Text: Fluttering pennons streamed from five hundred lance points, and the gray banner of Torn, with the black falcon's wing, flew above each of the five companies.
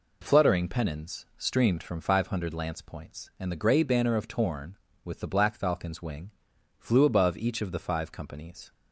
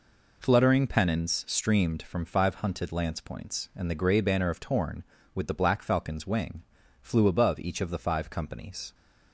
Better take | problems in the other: first | says "hunted" for "hundred"; at 2.5 s

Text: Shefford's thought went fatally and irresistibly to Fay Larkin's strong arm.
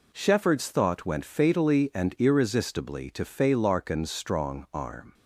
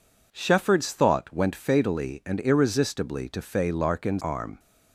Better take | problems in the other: first | skips "strong"; at 4.2 s

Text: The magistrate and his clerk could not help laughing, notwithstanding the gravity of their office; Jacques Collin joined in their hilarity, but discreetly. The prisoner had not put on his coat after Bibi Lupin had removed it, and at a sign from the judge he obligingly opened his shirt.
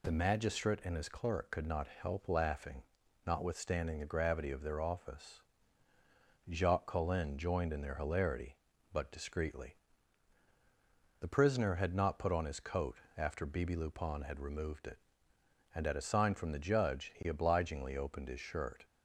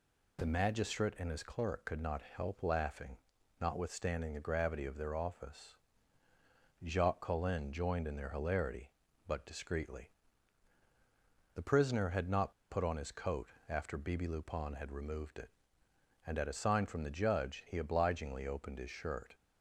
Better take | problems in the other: first | pauses between "not" and "put"; slight; at 12.5 s; 0.17 s long // pauses between "coat" and "after"; slight; at 13.4 s; 0.20 s long; slight in the first

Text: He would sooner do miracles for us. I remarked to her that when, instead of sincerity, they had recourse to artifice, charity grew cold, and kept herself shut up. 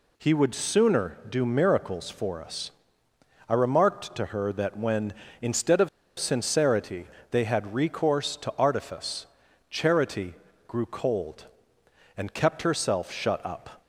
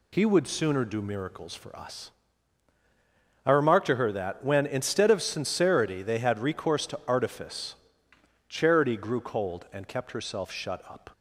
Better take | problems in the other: second | pauses between "of" and "sincerity"; slight; at 5.8 s; 0.30 s long // pauses between "charity" and "grew"; slight; at 10.3 s; 0.32 s long

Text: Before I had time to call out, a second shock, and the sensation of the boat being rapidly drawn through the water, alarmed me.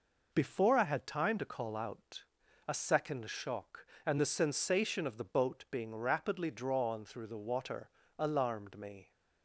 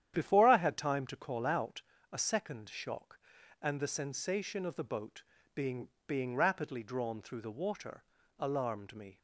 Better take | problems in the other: first | starts louder than the rest; strong; until 1.1 s; 10 dB // pauses between "boat" and "being"; slight; at 5.2 s; 0.32 s long // says "being" twice; at 6.0 s

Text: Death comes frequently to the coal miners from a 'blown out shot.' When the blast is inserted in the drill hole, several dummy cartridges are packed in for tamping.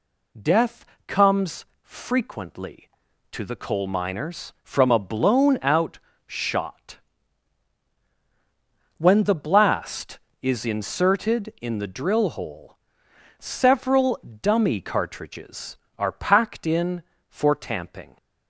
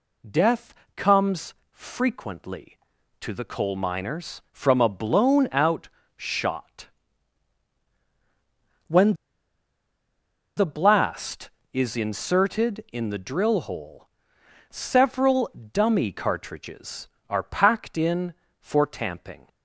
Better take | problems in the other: first | pauses between "Death" and "comes"; slight; at 0.7 s; 0.22 s long; slight in the first // pauses between "comes" and "frequently"; slight; at 1.5 s; 0.18 s long; slight in the first // pauses between "out" and "shot"; slight; at 5.8 s; 0.30 s long; slight in the first // pauses between "When" and "the"; strong; at 9.1 s; 1.4 s long // pauses between "several" and "dummy"; slight; at 15.4 s; 0.22 s long; slight in the first

